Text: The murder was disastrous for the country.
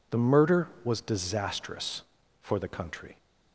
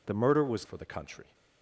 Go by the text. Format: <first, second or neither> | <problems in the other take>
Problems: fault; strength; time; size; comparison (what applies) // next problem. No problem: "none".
first | skips "disastrous"; at 0.6 s